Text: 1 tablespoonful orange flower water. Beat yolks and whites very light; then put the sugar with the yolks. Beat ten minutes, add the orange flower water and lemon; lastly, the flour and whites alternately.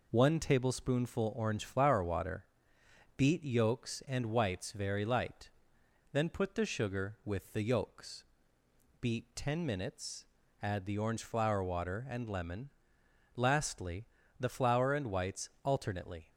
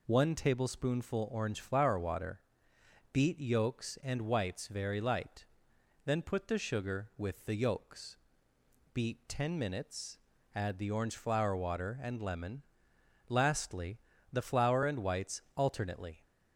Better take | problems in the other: second | gets quieter; slight; throughout; 2.5 dB // pauses between "whites" and "alternately"; slight; at 15.4 s; 0.16 s long; slight in the second

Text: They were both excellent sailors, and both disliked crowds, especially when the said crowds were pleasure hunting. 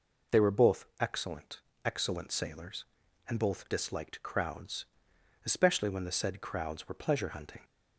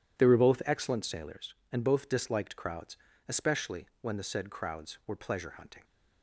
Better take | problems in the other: second | says "excellent" twice; at 1.8 s

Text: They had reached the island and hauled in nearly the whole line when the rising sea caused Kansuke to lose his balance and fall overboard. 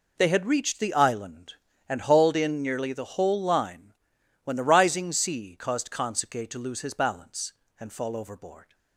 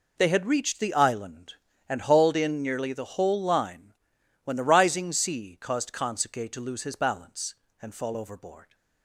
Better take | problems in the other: neither | pauses between "line" and "when"; noticeable; the same in both

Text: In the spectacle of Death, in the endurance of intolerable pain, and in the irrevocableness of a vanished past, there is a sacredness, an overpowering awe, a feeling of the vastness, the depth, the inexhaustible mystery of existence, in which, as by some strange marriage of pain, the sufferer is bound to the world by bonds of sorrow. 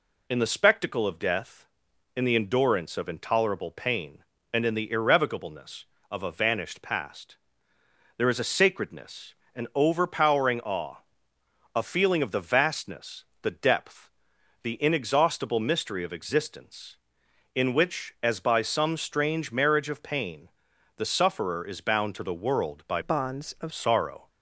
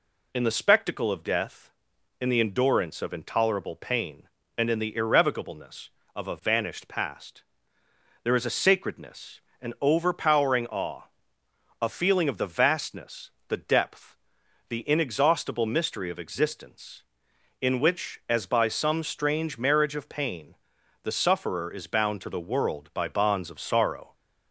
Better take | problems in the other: second | changes voice from "bonds" to "of"; from 23.0 to 23.7 s; 0.7 s long

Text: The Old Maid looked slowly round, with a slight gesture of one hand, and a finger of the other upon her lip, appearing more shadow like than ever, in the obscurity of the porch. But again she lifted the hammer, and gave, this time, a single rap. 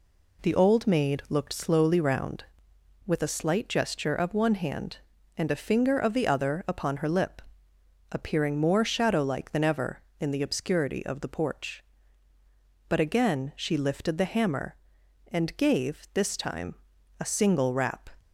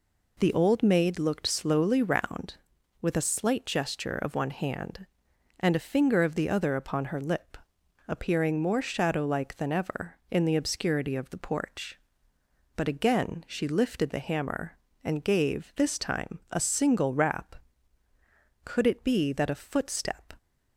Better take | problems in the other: first | goes on to say "Could it be that a footstep"; strong; from 18.6 s on; 1.7 s long

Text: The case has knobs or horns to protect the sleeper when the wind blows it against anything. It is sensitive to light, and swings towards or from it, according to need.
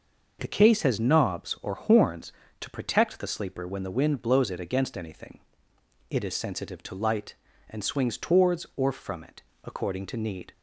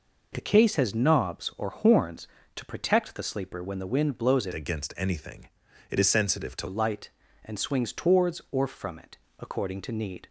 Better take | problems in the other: first | changes voice from "against" to "to"; from 4.5 to 6.6 s; 2.1 s long

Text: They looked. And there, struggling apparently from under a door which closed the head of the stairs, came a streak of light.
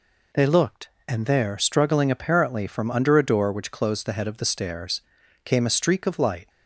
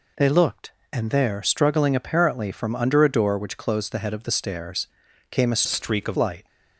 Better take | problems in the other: first | changes voice from "streak" to "of"; from 5.6 to 6.1 s; 0.5 s long

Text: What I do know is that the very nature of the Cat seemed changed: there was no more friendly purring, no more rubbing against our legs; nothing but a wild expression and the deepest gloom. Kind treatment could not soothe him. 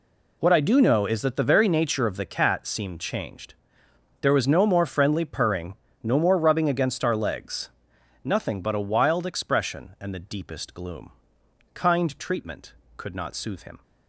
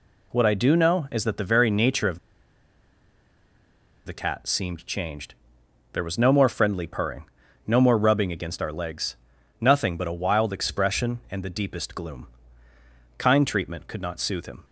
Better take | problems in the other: first | pauses between "of" and "the"; strong; at 2.1 s; 1.8 s long

